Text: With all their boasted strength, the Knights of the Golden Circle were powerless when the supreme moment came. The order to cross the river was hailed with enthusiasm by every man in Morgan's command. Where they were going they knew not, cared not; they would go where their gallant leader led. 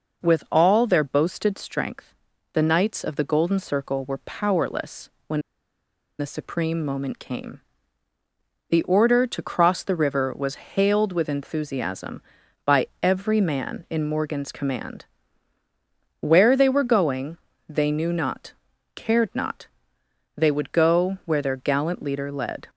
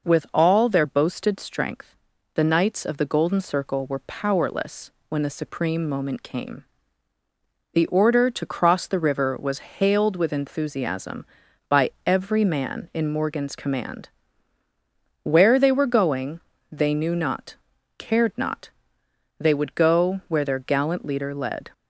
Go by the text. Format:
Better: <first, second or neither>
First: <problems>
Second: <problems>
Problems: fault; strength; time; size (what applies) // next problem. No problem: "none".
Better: second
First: pauses between "powerless" and "when"; slight; at 5.0 s; 0.16 s long // pauses between "when" and "the"; noticeable; at 5.3 s; 0.79 s long // pauses between "going" and "they"; slight; at 17.3 s; 0.28 s long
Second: pauses between "powerless" and "when"; slight; at 4.9 s; 0.16 s long // pauses between "going" and "they"; slight; at 16.4 s; 0.28 s long